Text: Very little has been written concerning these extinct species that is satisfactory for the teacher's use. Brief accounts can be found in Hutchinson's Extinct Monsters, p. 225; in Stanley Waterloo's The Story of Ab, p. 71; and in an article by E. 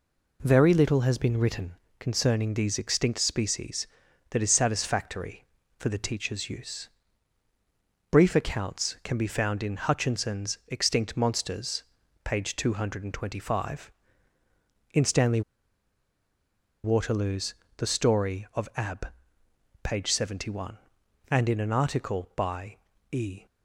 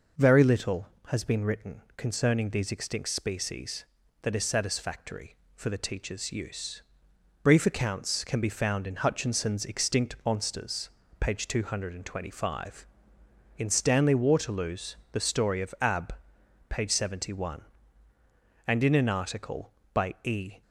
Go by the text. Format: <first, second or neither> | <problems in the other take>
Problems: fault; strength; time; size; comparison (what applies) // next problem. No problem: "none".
second | pauses between "written" and "concerning"; slight; at 1.7 s; 0.24 s long; slight in the second // pauses between "Stanley" and "Waterloo's"; strong; at 15.4 s; 1.4 s long // pauses between "Waterloo's" and "The"; slight; at 17.5 s; 0.22 s long; slight in the second // pauses between "by" and "E"; slight; at 22.7 s; 0.34 s long